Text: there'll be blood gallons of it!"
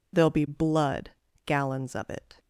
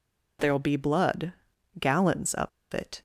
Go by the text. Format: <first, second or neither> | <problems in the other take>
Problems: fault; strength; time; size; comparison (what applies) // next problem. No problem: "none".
first | pauses between "blood" and "gallons"; noticeable; at 1.3 s; 0.46 s long; slight in the first // pauses between "of" and "it"; slight; at 2.4 s; 0.24 s long